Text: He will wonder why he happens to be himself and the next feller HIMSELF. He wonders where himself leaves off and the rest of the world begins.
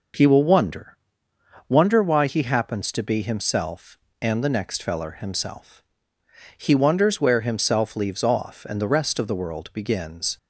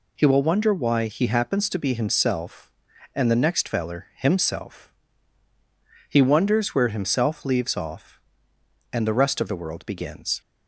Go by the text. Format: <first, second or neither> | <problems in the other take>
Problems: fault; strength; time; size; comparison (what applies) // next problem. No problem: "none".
second | says "wonder" twice; at 1.6 s